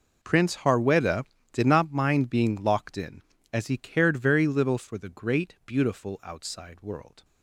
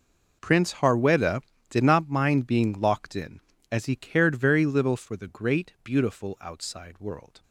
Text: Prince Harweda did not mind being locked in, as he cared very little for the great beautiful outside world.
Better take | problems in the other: neither | none

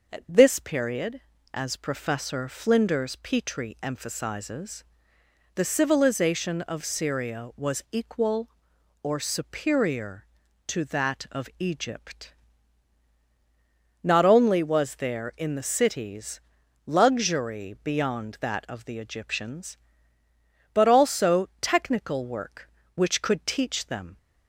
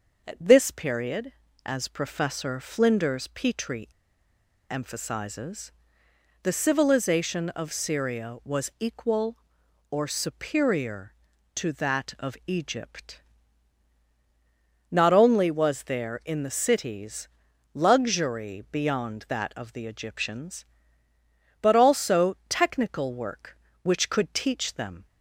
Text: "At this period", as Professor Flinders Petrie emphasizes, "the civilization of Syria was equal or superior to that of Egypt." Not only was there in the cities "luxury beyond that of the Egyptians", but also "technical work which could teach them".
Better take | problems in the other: first | pauses between "Petrie" and "emphasizes"; noticeable; at 3.8 s; 0.80 s long // pauses between "cities" and "luxury"; at 17.2 s; 0.44 s long; also in the first

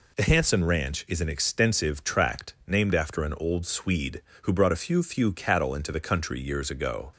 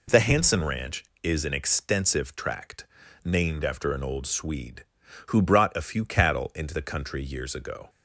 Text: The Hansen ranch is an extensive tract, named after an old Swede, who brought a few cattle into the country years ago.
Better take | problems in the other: second | says "few" twice; at 5.0 s

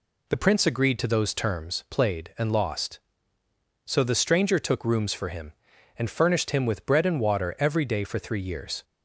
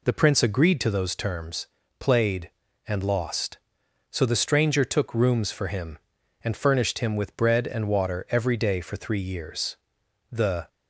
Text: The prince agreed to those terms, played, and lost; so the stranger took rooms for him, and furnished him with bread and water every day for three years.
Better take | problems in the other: first | goes on to say "The"; slight; from 10.2 s on; 0.38 s long

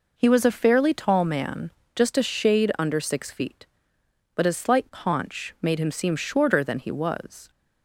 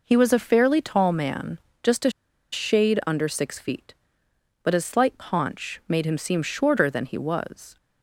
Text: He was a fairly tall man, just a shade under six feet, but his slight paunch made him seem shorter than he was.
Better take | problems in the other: first | pauses between "a" and "shade"; at 2.0 s; 0.42 s long

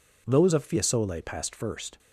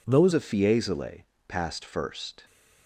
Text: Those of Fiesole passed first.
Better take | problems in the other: first | changes voice at "of"; from 0.3 s on; 2.1 s long // pauses between "Fiesole" and "passed"; slight; at 1.2 s; 0.24 s long

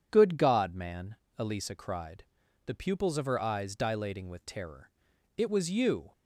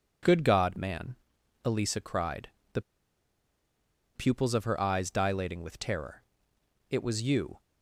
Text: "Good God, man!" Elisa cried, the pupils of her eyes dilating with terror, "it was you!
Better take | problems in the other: first | pauses between "the" and "pupils"; strong; at 2.7 s; 1.3 s long

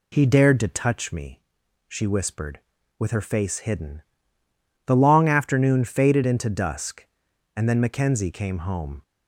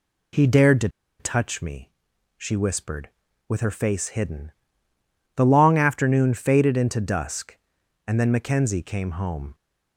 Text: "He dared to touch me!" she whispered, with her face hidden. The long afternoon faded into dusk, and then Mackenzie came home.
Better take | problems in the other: first | pauses between "to" and "touch"; slight; at 0.8 s; 0.31 s long

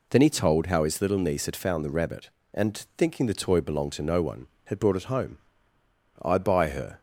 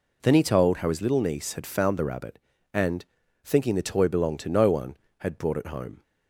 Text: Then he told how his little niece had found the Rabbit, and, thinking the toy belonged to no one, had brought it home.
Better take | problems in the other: second | goes on to say "I buy her"; noticeable; from 6.2 s on; 0.78 s long

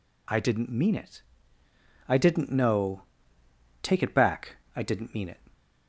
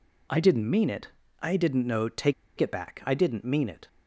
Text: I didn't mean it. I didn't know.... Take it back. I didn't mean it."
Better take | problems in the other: first | pauses between "Take" and "it"; slight; at 2.3 s; 0.25 s long

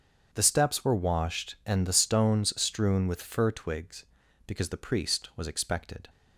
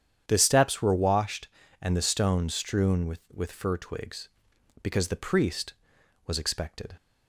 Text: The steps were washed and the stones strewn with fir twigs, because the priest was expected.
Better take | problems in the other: first | starts louder than the rest; strong; until 1.2 s; 9 dB; strong in the first // says "with" twice; at 3.3 s

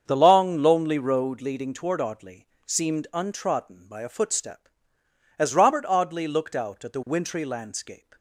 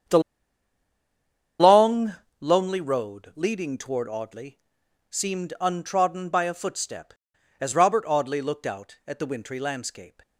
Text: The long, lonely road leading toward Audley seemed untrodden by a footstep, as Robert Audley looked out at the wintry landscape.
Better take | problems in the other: first | starts louder than the rest; strong; until 2.7 s; 8 dB; strong in the first // pauses between "The" and "long"; strong; at 0.2 s; 1.3 s long // pauses between "Audley" and "seemed"; noticeable; at 4.5 s; 0.50 s long; slight in the first

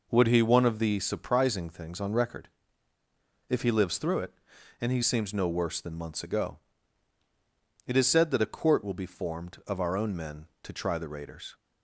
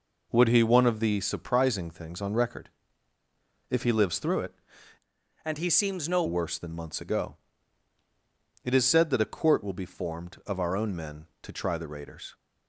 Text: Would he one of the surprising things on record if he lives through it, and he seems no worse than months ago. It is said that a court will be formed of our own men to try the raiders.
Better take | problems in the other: first | pauses between "record" and "if"; at 2.6 s; 1.0 s long; also in the first // changes voice from "and" to "no"; from 5.4 to 6.2 s; 0.8 s long

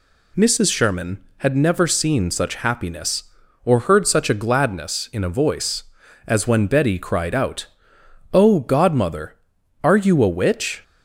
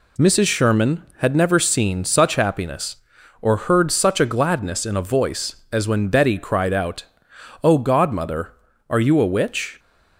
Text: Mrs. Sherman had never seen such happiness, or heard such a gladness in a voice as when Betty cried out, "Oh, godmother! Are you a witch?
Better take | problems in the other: neither | none

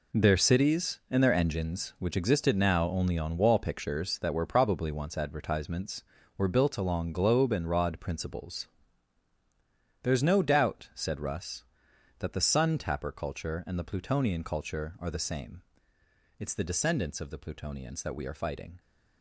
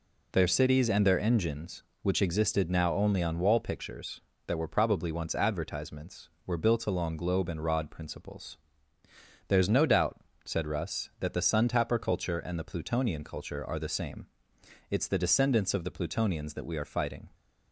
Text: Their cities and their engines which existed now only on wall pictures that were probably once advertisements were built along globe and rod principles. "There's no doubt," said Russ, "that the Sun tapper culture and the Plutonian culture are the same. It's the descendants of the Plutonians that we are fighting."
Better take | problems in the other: second | gets quieter; strong; throughout; 11 dB

